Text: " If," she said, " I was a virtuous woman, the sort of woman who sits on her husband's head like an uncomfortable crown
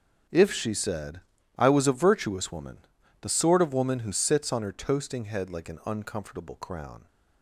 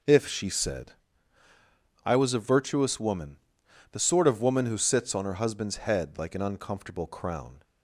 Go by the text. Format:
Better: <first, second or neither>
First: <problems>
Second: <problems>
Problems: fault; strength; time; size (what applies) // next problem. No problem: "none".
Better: second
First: says "toasting" for "husband's"; at 4.7 s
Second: none